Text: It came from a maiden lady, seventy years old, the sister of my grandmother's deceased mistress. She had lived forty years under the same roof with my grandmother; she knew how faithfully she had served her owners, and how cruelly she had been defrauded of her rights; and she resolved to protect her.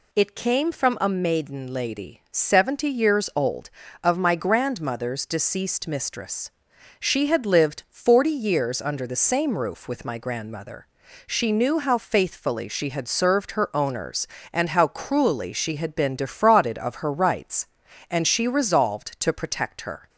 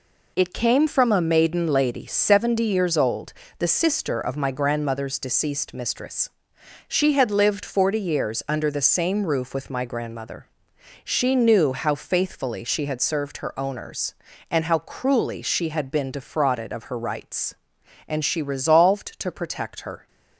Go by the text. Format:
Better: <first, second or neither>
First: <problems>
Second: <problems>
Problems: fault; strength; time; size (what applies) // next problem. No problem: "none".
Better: second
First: skips "the sister"; at 3.8 s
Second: none